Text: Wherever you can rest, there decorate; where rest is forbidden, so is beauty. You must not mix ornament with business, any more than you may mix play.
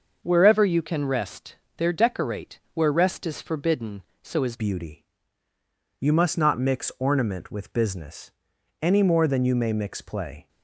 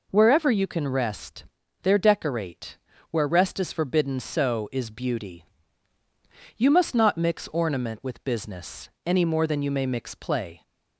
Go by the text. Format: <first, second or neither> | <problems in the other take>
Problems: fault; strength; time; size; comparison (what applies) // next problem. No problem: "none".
second | starts louder than the rest; noticeable; until 1.2 s; 6 dB // changes voice at "beauty"; from 4.5 s on; 5.9 s long